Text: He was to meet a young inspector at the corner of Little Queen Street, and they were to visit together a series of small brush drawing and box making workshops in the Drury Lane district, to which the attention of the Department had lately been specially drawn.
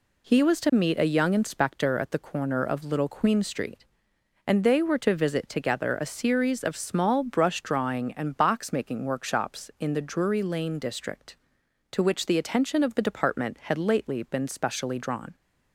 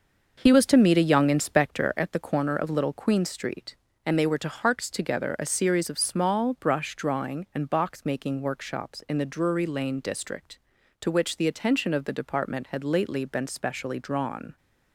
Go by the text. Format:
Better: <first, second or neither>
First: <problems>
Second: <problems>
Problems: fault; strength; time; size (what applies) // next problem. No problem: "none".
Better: first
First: none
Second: starts louder than the rest; until 1.4 s; 6 dB // says "harks" for "visit"; at 4.4 s